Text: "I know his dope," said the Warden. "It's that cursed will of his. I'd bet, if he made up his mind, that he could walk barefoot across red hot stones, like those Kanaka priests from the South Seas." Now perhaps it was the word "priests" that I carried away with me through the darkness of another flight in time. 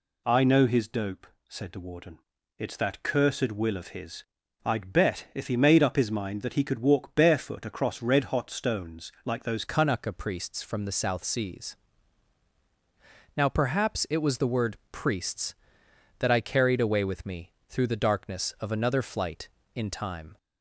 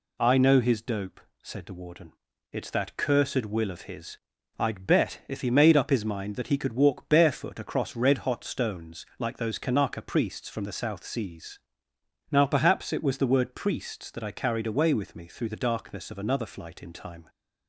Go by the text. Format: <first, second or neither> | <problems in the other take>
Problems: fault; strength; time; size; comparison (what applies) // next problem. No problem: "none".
second | changes voice at "Kanaka"; from 9.6 s on; 10.7 s long // pauses between "me" and "through"; slight; at 17.5 s; 0.18 s long